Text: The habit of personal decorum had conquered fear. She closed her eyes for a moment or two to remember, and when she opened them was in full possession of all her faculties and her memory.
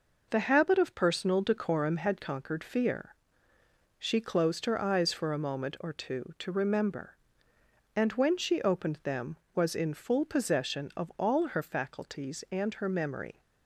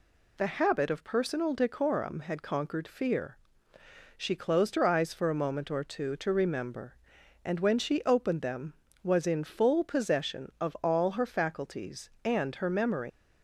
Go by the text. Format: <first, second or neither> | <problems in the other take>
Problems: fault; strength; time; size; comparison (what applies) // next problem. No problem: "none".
first | leaves "memory" unfinished; at 13.1 s; 105 ms